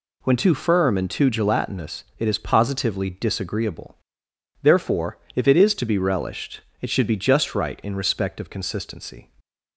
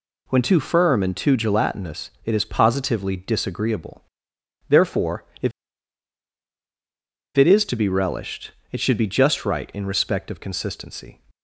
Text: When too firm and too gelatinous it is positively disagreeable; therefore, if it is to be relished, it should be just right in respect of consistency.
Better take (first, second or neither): first